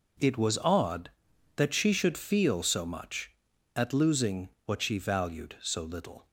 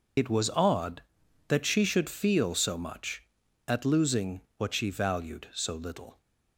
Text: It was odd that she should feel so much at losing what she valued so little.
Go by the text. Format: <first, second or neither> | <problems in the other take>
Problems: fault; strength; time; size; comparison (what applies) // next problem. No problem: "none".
first | loses the start of "It"; at 0.1 s; 80 ms // pauses between "losing" and "what"; slight; at 4.4 s; 0.18 s long; slight in the first